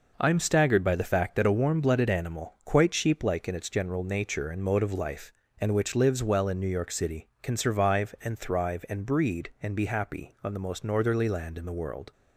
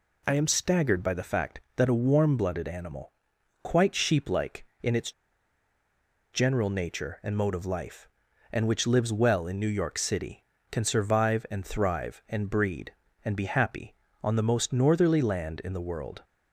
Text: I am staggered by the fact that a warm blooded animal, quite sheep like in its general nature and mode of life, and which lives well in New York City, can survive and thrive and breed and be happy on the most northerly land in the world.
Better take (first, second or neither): first